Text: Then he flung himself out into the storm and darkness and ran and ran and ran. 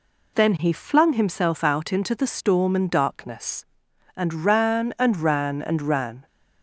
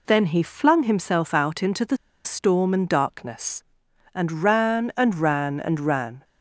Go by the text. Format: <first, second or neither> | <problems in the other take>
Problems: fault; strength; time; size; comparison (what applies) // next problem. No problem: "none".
first | pauses between "the" and "storm"; slight; at 1.9 s; 0.28 s long